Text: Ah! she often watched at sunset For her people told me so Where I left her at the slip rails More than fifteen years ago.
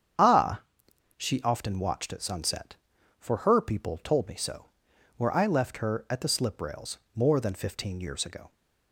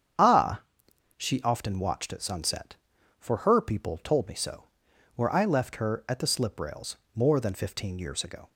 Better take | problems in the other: neither | starts louder than the rest; strong; the same in both // pauses between "so" and "Where"; noticeable; the same in both // pauses between "rails" and "More"; slight; the same in both

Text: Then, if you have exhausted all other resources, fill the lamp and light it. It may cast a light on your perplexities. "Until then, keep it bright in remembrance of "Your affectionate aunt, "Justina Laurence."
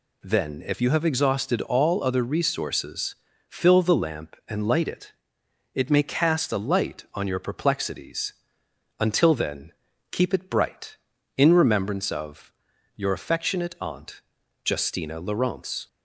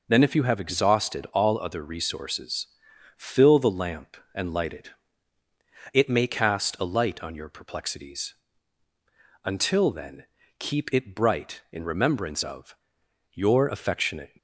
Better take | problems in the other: first | pauses between "of" and "Your"; noticeable; at 12.7 s; 0.56 s long; also in the first // stops before "aunt Justina Laurence"; at 14.3 s

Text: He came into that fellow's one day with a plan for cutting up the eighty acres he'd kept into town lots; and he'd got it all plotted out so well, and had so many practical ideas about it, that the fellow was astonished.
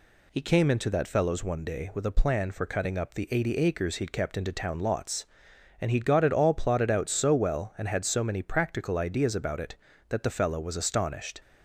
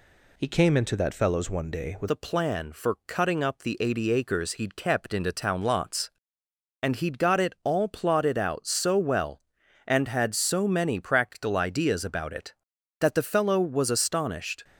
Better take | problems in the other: first | changes voice at "a"; from 2.0 s on; 12.6 s long

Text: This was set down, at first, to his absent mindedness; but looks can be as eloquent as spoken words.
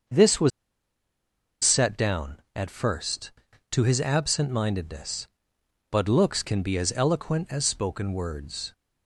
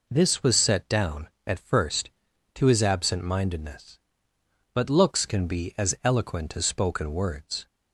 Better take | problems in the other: second | starts louder than the rest; until 2.2 s; 6.5 dB // pauses between "was" and "set"; at 0.5 s; 1.1 s long

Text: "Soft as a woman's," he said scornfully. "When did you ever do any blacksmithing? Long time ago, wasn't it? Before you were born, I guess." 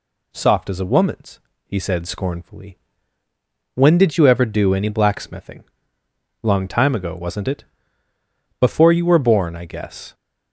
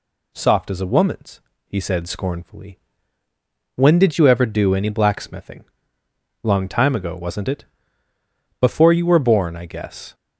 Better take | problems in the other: neither | none

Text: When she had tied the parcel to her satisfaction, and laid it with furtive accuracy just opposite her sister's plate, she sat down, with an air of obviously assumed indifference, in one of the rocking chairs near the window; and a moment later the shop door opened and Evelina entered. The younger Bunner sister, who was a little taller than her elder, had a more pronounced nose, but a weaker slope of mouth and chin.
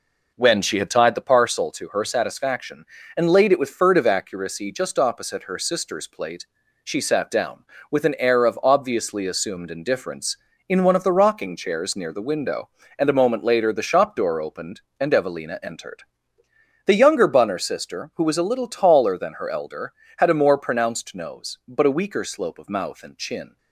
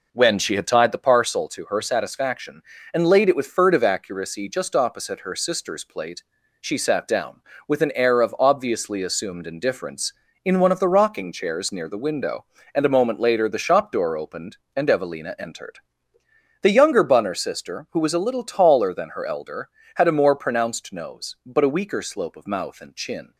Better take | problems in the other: neither | none

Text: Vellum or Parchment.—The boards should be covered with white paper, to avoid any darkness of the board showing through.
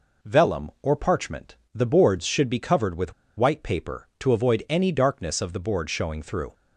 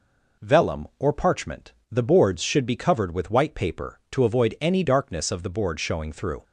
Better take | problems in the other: second | pauses between "with" and "white"; slight; at 3.1 s; 0.25 s long

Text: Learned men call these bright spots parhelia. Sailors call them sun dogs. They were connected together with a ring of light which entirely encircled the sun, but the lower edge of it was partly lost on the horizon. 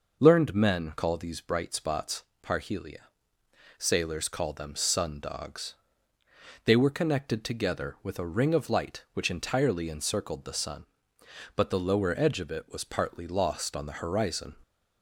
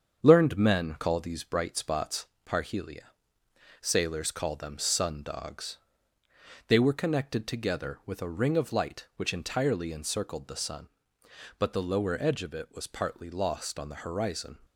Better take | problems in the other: first | gets quieter; noticeable; throughout; 4.5 dB // pauses between "spots" and "parhelia"; slight; at 2.2 s; 0.24 s long; slight in the first

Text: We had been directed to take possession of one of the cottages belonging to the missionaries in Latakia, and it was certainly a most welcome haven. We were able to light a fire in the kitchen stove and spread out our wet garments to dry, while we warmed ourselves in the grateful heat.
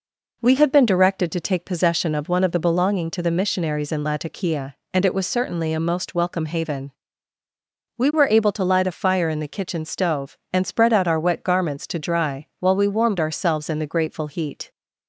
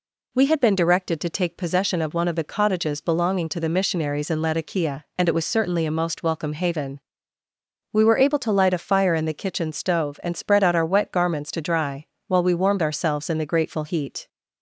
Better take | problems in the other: second | skips "cottages"; at 2.6 s

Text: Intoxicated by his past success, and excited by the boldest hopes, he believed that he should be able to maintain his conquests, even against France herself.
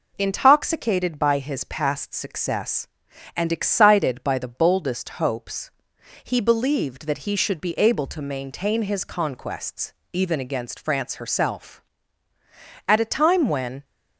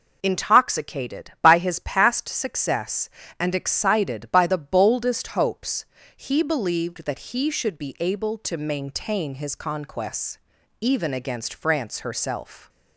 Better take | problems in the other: second | goes on to say "At a time when"; noticeable; from 12.8 s on; 0.98 s long

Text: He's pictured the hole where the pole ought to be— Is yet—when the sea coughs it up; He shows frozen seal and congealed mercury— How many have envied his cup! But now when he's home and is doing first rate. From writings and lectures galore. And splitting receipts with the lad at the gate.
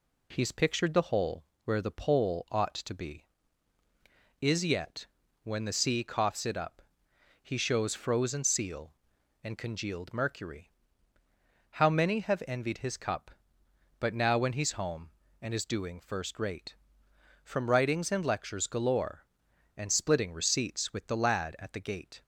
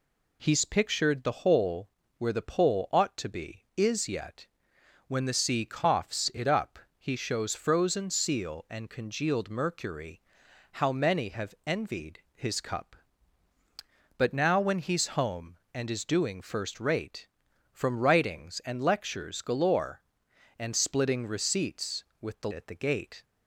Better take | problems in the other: first | pauses between "hole" and "where"; slight; at 1.8 s; 0.30 s long; slight in the first // skips "lad"; at 22.5 s

